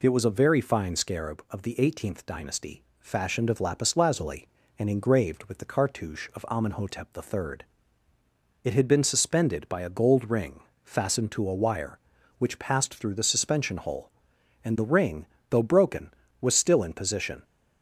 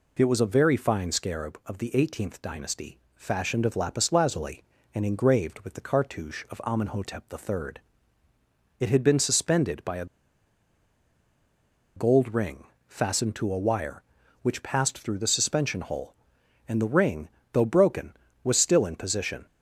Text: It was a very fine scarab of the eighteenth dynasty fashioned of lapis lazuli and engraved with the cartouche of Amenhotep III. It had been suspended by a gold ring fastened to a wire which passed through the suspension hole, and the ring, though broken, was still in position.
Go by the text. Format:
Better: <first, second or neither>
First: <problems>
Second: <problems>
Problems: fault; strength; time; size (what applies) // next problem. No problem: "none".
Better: first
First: pauses between "dynasty" and "fashioned"; slight; at 2.8 s; 0.16 s long // pauses between "ring" and "fastened"; slight; at 10.6 s; 0.20 s long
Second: pauses between "dynasty" and "fashioned"; slight; at 2.9 s; 0.16 s long // pauses between "a" and "gold"; strong; at 10.0 s; 1.9 s long // pauses between "ring" and "fastened"; slight; at 12.6 s; 0.20 s long